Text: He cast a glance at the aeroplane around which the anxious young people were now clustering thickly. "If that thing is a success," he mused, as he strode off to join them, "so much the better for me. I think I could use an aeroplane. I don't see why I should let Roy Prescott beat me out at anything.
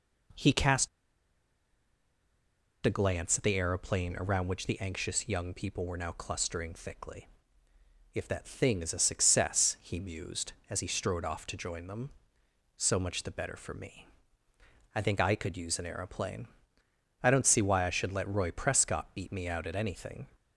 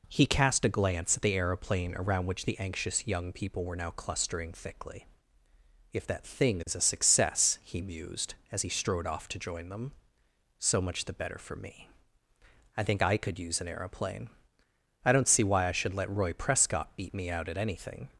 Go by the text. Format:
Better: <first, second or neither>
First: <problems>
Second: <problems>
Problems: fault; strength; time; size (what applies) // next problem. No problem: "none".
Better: second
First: pauses between "cast" and "a"; strong; at 0.8 s; 1.9 s long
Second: none